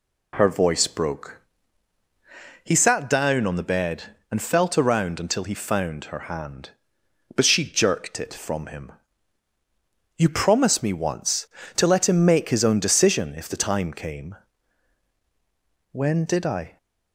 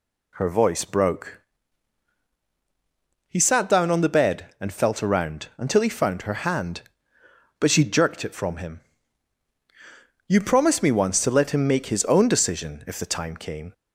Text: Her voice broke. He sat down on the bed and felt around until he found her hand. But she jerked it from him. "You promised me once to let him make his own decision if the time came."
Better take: second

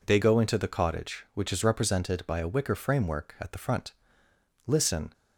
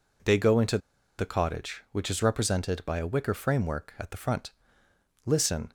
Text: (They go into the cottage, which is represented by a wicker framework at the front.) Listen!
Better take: first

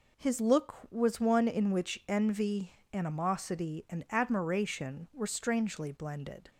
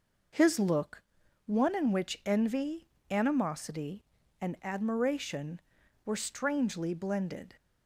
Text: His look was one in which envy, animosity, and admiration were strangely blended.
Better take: first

